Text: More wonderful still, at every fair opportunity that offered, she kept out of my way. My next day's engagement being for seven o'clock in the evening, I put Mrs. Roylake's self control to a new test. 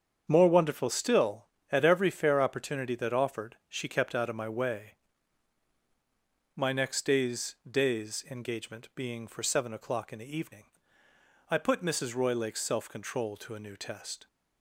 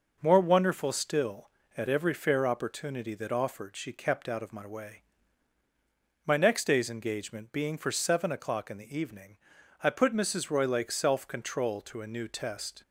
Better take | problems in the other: second | starts louder than the rest; strong; until 1.2 s; 7.5 dB // says "day's" twice; at 7.6 s

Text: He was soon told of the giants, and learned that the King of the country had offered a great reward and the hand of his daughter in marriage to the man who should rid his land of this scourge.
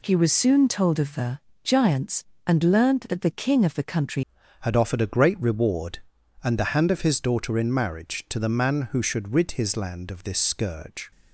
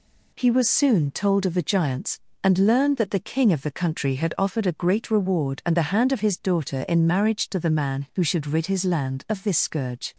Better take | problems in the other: second | pauses between "the" and "giants"; slight; at 1.3 s; 0.26 s long // changes voice at "had"; from 4.6 s on; 6.5 s long

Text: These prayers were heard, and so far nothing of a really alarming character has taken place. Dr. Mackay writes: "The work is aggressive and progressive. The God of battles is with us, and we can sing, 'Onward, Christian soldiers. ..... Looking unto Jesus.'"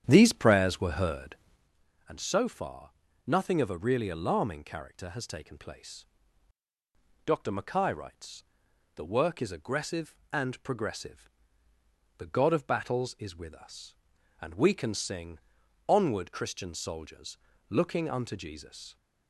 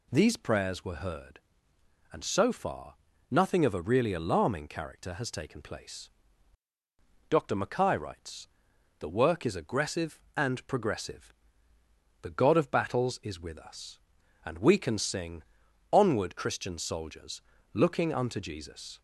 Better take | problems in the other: second | starts louder than the rest; strong; until 1.7 s; 9 dB // pauses between "far" and "nothing"; slight; at 2.8 s; 0.36 s long; slight in the second

